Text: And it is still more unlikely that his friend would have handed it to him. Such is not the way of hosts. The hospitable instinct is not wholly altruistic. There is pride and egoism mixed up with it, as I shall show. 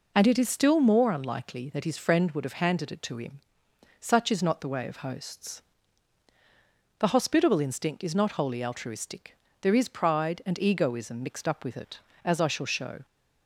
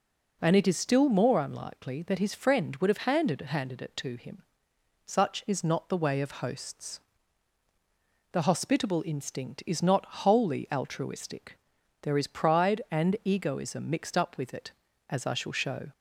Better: first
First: none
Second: says "handed" twice; at 3.4 s

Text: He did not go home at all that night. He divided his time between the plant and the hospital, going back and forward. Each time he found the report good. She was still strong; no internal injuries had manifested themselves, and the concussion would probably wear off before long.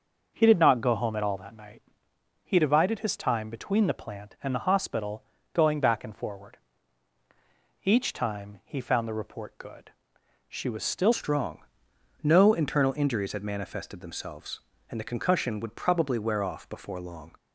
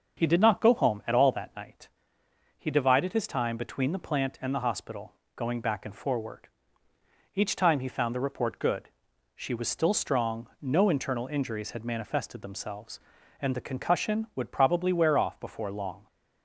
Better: second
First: starts louder than the rest; noticeable; until 1.3 s; 6 dB // changes voice at "strong"; from 11.1 s on; 6.2 s long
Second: starts louder than the rest; until 1.2 s; 6.5 dB

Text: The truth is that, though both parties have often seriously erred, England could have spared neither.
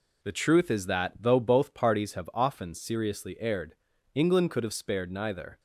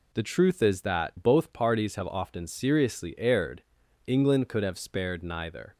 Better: first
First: none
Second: skips "though"; at 1.1 s

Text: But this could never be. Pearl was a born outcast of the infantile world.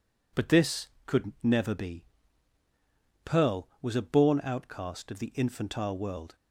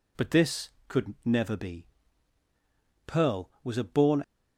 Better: first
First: none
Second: stops before "outcast of the infantile world"; at 4.2 s

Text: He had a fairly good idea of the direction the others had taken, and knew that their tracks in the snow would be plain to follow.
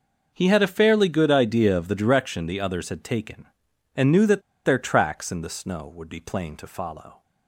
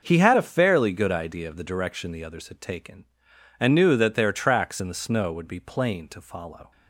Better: second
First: pauses between "that" and "their"; slight; at 4.4 s; 0.23 s long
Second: none

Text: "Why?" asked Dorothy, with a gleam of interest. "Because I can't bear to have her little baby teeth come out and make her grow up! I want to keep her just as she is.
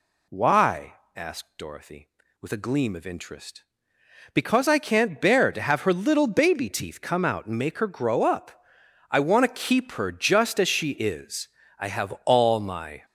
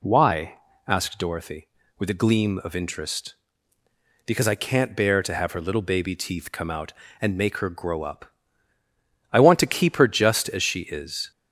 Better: second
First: goes on to say "I have all my"; noticeable; from 11.7 s on; 1.2 s long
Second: none

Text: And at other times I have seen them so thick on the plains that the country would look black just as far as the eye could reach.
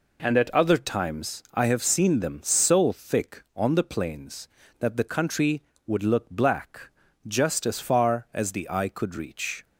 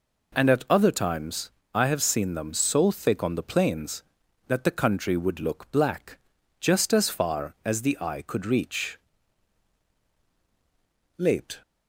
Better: first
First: pauses between "black" and "just"; slight; at 6.9 s; 0.36 s long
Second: pauses between "times" and "I"; slight; at 1.4 s; 0.24 s long // pauses between "black" and "just"; at 6.1 s; 0.42 s long // goes on to say "Late"; slight; from 11.1 s on; 0.44 s long

